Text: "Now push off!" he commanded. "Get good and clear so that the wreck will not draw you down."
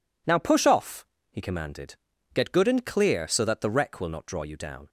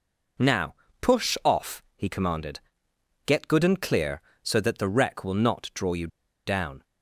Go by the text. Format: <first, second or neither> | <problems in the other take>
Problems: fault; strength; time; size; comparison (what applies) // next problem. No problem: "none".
first | pauses between "Now" and "push"; slight; at 0.7 s; 0.26 s long // pauses between "you" and "down"; at 6.0 s; 0.39 s long